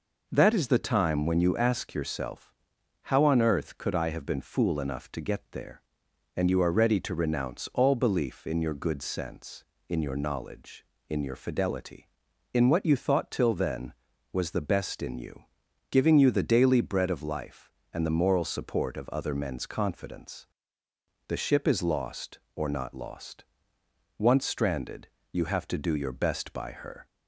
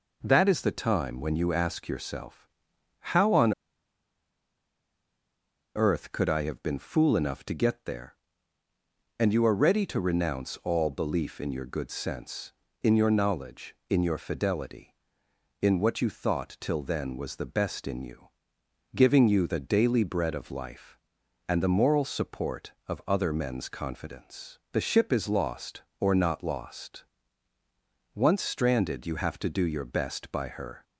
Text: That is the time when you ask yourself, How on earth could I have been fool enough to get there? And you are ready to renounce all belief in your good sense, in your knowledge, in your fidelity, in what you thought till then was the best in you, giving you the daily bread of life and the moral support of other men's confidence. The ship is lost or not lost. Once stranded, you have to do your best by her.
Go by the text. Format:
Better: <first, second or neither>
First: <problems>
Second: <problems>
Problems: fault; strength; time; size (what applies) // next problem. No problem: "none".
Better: first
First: none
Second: pauses between "on" and "earth"; strong; at 3.5 s; 2.2 s long